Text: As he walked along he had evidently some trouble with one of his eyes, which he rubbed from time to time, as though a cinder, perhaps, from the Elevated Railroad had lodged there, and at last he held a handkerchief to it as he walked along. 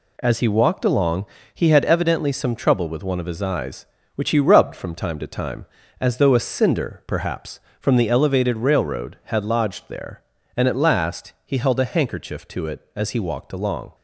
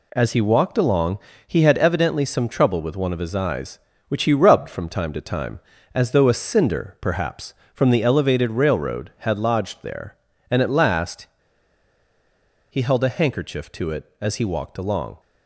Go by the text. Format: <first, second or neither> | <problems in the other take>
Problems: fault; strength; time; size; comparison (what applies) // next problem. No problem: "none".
first | pauses between "along" and "he"; slight; at 1.1 s; 0.26 s long; slight in the first // pauses between "last" and "he"; strong; at 11.2 s; 1.4 s long